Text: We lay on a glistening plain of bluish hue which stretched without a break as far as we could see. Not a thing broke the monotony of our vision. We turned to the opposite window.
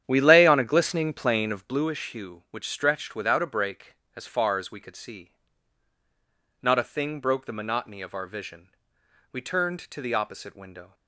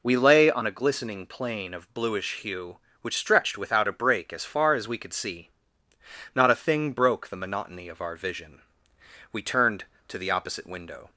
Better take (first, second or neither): second